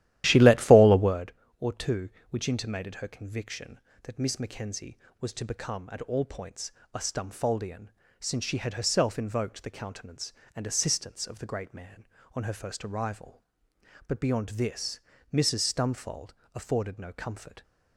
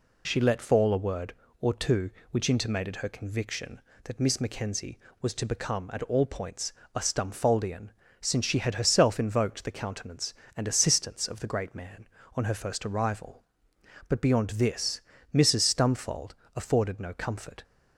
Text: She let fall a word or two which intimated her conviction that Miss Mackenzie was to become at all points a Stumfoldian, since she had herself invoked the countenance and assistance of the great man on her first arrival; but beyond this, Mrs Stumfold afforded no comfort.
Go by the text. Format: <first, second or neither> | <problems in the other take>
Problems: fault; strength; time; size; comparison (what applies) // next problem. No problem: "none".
second | starts louder than the rest; strong; until 1.3 s; 13.5 dB // pauses between "points" and "a"; slight; at 6.7 s; 0.24 s long; slight in the second // pauses between "Stumfold" and "afforded"; slight; at 16.3 s; 0.22 s long; slight in the second